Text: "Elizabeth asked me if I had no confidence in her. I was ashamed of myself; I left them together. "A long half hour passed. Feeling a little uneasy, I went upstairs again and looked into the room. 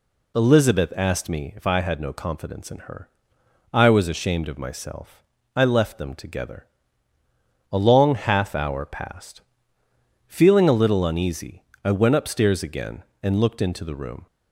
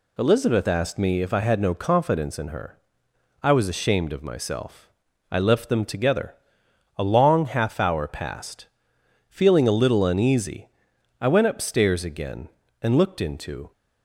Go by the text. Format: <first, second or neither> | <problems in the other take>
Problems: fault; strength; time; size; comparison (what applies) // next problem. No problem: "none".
first | stops before "the room"; at 13.7 s